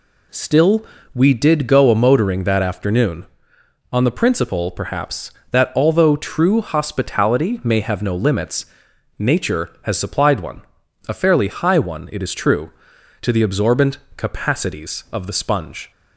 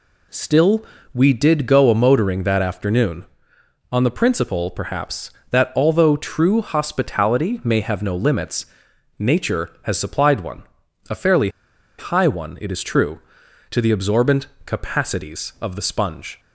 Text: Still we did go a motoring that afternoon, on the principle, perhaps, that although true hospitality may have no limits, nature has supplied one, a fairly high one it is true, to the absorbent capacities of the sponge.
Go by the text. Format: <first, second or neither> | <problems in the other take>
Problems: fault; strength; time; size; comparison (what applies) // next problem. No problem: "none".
first | pauses between "Still" and "we"; slight; at 0.8 s; 0.30 s long; slight in the first // pauses between "fairly" and "high"; noticeable; at 11.4 s; 0.50 s long // pauses between "absorbent" and "capacities"; slight; at 14.4 s; 0.18 s long; slight in the first